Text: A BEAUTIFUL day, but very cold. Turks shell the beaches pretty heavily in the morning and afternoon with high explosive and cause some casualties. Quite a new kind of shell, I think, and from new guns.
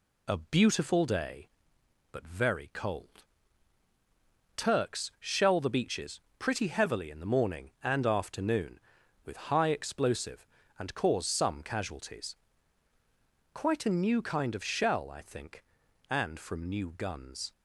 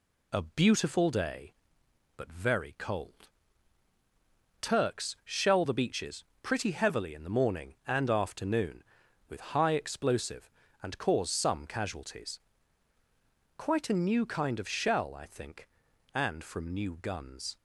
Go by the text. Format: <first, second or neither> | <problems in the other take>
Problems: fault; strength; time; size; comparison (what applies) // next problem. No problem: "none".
neither | pauses between "beaches" and "pretty"; slight; the same in both